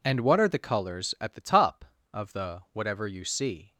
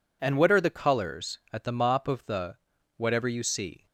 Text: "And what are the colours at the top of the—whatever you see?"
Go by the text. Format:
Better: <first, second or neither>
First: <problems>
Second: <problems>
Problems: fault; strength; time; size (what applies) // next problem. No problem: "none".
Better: first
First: none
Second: says "mop" for "top"; at 1.7 s